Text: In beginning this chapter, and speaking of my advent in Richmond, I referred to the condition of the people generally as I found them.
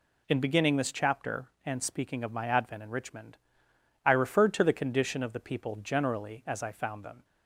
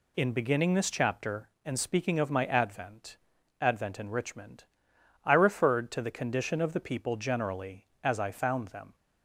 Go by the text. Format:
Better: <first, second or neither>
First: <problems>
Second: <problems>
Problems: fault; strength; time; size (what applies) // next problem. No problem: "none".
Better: first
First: none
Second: says "advent" twice; at 3.6 s